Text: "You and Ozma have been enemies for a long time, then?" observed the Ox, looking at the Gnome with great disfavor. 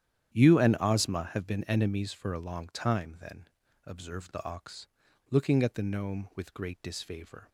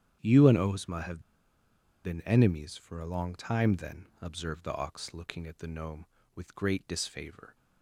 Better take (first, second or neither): first